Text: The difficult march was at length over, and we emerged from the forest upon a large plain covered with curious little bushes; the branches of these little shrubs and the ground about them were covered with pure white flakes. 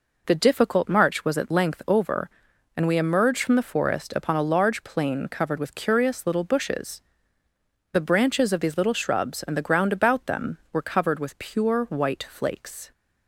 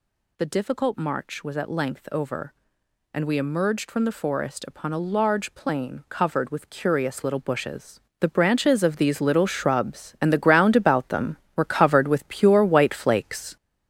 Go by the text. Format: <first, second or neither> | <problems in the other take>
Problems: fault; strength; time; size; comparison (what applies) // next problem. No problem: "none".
first | gets louder; throughout; 6.5 dB